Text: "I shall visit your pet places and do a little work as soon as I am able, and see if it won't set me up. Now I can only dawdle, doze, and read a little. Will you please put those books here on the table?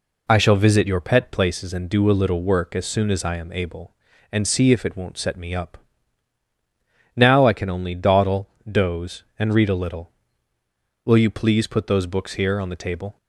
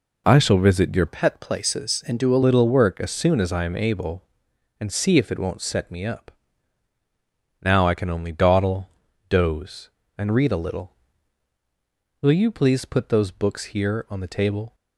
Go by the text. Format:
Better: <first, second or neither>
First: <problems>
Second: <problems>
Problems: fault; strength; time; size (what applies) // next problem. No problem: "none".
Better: first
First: none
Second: changes voice from "pet" to "a"; from 1.0 to 2.4 s; 1.4 s long